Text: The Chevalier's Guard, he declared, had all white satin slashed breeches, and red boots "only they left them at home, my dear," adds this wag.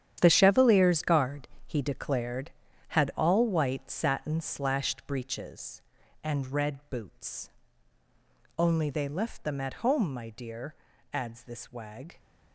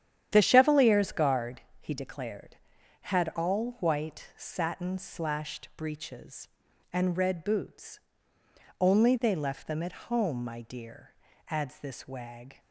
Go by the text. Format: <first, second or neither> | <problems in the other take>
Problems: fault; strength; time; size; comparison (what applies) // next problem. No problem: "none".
second | gets quieter; strong; throughout; 12 dB // starts louder than the rest; strong; until 1.2 s; 10 dB; strong in the second // pauses between "boots" and "only"; at 7.4 s; 1.0 s long; noticeable in the second